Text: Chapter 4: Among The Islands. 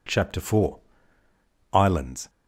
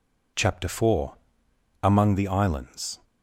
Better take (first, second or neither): second